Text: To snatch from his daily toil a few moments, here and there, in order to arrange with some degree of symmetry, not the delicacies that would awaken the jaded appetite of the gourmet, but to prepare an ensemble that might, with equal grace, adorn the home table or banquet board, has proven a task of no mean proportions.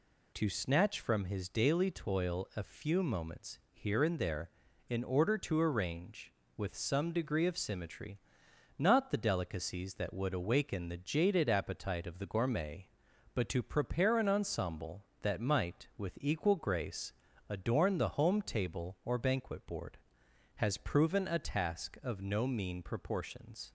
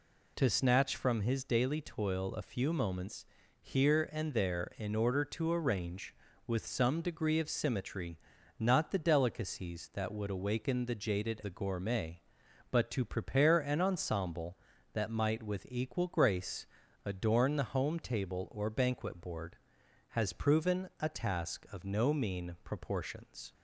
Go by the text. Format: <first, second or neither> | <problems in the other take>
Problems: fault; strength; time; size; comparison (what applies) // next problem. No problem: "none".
first | skips "appetite of"; at 11.4 s